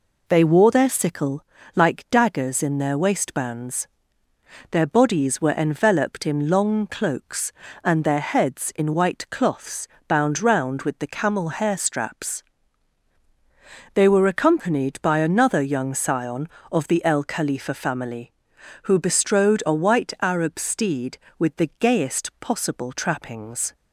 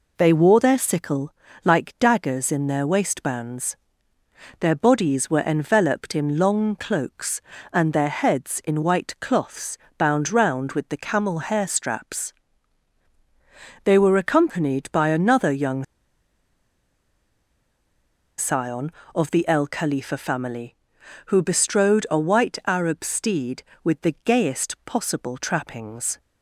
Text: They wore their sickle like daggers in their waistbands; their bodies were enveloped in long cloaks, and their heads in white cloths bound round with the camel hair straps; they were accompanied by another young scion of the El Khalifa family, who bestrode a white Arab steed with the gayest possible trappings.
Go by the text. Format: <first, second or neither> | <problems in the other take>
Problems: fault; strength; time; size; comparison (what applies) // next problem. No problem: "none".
first | pauses between "sickle" and "like"; slight; at 1.3 s; 0.32 s long; slight in the first // pauses between "cloths" and "bound"; slight; at 9.7 s; 0.22 s long; slight in the first // pauses between "young" and "scion"; strong; at 15.8 s; 2.5 s long